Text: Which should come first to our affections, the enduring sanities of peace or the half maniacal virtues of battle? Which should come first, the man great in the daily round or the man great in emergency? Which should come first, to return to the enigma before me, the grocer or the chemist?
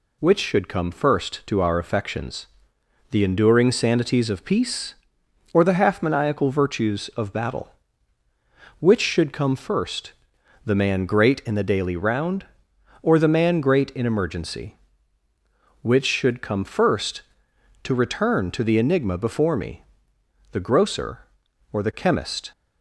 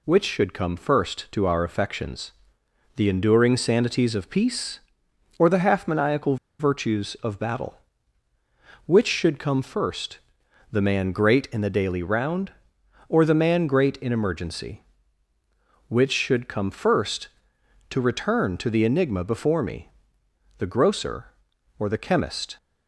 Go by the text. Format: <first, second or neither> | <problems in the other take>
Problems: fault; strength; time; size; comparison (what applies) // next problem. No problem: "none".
first | pauses between "maniacal" and "virtues"; slight; at 6.3 s; 0.23 s long